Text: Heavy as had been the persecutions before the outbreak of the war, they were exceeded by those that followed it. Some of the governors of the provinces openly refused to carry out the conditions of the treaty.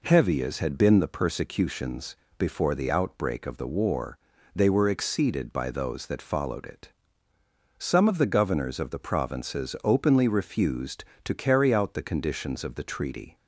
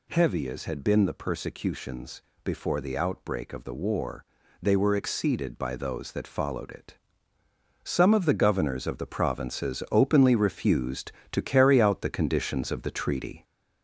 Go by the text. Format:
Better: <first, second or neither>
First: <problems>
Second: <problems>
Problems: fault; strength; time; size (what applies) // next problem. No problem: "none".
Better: first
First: pauses between "persecutions" and "before"; slight; at 2.1 s; 0.20 s long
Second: gets louder; noticeable; throughout; 4 dB // pauses between "persecutions" and "before"; slight; at 2.2 s; 0.20 s long